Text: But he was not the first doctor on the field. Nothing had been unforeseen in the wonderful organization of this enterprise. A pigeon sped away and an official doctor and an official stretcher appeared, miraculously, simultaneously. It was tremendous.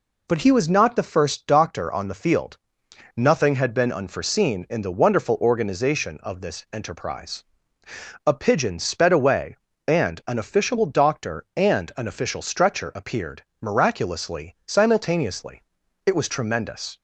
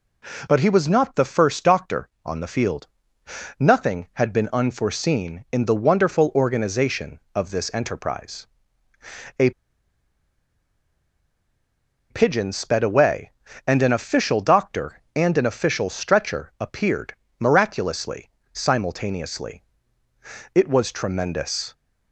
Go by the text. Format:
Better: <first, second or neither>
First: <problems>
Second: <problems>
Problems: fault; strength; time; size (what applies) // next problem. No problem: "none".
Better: first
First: none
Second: pauses between "A" and "pigeon"; strong; at 9.5 s; 2.6 s long